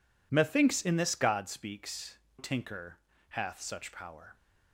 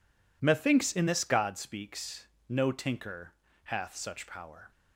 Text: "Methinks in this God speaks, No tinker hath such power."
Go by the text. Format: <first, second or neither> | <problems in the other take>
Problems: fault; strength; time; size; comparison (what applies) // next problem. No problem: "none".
second | skips "No"; at 2.2 s // pauses between "tinker" and "hath"; slight; at 2.9 s; 0.32 s long; slight in the second